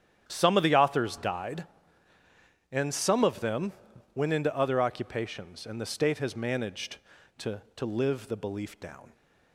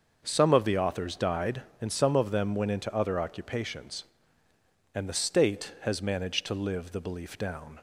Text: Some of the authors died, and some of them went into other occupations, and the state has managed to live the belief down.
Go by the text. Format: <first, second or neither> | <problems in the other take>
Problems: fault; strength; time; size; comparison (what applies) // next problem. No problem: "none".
second | starts louder than the rest; strong; until 1.2 s; 9.5 dB; also in the second // pauses between "them" and "went"; at 3.7 s; 0.42 s long // says "to" twice; at 7.7 s